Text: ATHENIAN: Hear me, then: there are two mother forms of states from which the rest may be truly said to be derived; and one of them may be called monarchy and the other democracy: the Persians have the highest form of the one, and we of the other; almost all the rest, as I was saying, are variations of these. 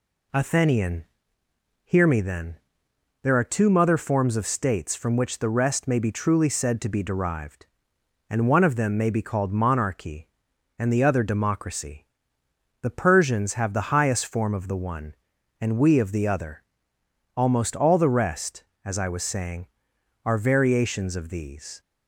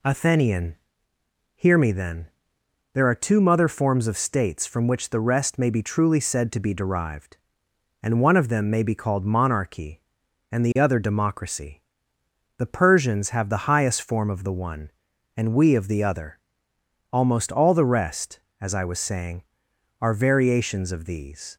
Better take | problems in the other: neither | none

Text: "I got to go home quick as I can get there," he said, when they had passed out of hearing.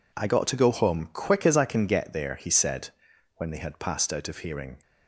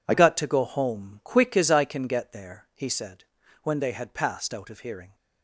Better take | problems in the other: first | changes voice at "got"; from 0.1 s on; 5.0 s long

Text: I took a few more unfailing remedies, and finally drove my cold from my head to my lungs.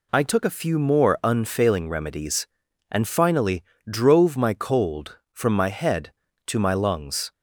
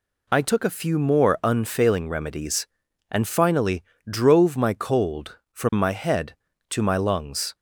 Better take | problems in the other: neither | pauses between "finally" and "drove"; slight; the same in both

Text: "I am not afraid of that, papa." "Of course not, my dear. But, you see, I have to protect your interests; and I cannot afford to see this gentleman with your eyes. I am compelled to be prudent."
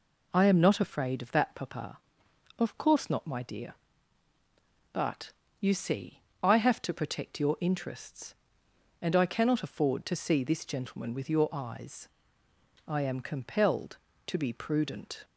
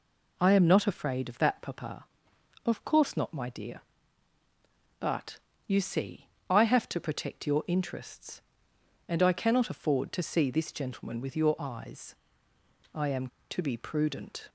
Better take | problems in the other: first | skips "compelled"; at 13.3 s

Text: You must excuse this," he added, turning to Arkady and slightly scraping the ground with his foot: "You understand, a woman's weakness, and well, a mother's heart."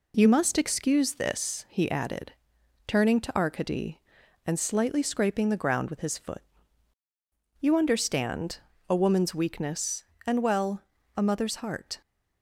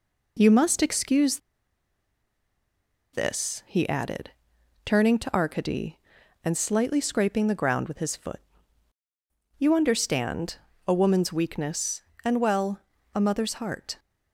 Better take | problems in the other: first | pauses between "excuse" and "this"; strong; at 1.3 s; 1.7 s long

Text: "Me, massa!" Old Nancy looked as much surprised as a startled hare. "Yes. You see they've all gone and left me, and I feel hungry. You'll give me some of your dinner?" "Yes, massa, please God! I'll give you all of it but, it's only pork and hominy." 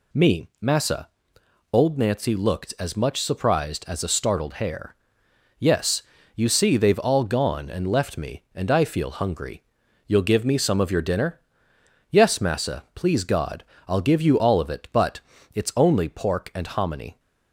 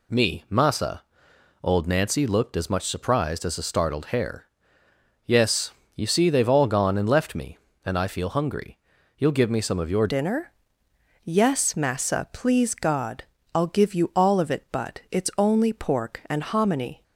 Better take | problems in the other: first | changes voice at "dinner"; from 10.0 s on; 7.0 s long

